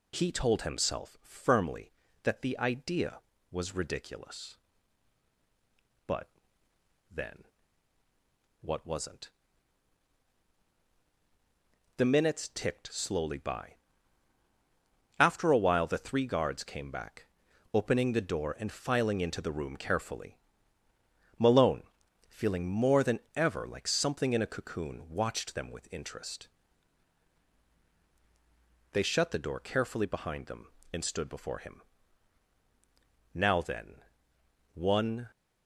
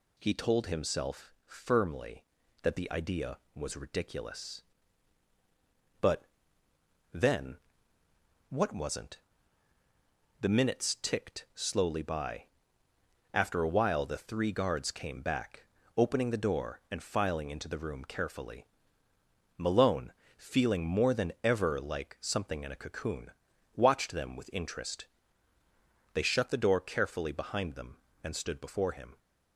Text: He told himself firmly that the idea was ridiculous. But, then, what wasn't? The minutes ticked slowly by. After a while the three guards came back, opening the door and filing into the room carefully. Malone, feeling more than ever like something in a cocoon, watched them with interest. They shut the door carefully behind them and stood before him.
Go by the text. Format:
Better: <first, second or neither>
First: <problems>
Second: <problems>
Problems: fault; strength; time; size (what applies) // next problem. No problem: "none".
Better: second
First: pauses between "than" and "ever"; slight; at 23.1 s; 0.16 s long // goes on to say "Now then one"; strong; from 33.3 s on; 1.9 s long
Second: none